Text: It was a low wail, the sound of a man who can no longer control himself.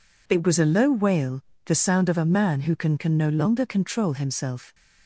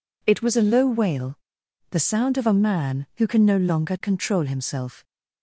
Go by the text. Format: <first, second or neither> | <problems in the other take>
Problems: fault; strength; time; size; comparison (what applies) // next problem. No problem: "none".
second | says "can" twice; at 2.9 s